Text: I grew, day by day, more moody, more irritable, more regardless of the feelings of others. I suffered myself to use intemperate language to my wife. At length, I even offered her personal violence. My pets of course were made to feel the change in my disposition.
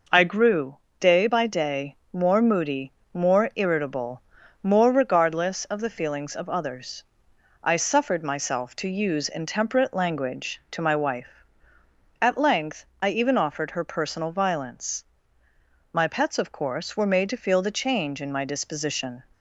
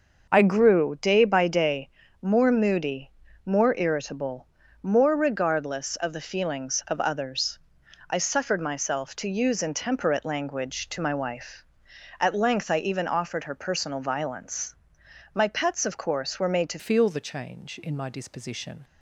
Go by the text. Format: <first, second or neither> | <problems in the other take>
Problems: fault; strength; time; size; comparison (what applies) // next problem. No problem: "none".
first | starts louder than the rest; noticeable; until 1.3 s; 6 dB // changes voice at "feel"; from 16.7 s on; 2.1 s long